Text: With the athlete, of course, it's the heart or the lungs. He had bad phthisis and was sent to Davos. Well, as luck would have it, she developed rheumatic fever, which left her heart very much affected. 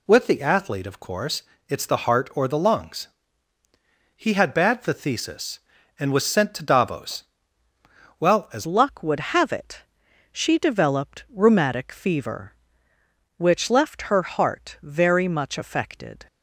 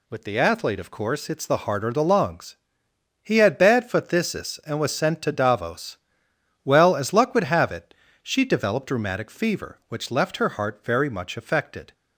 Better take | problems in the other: second | changes voice at "luck"; from 8.6 s on; 7.6 s long

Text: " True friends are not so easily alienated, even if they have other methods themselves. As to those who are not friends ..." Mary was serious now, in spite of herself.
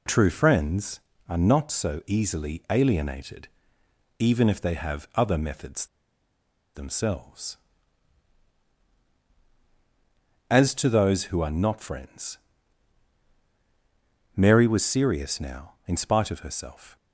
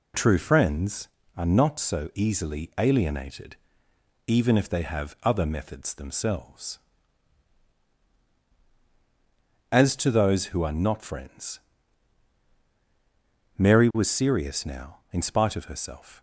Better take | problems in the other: second | pauses between "methods" and "themselves"; noticeable; at 5.8 s; 0.89 s long

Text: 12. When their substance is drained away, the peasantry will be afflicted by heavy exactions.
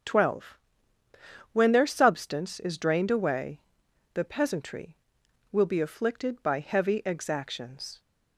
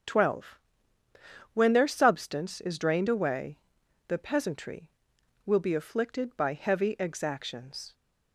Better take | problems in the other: neither | starts louder than the rest; the same in both

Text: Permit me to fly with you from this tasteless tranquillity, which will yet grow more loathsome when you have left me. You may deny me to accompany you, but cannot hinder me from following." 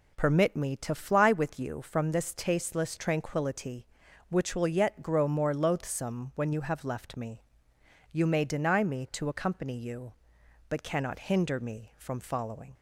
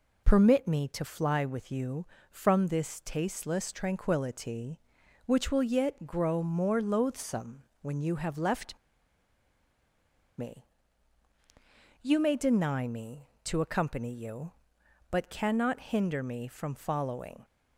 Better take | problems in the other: first | pauses between "loathsome" and "when"; slight; at 7.6 s; 0.20 s long // pauses between "left" and "me"; strong; at 8.7 s; 1.6 s long

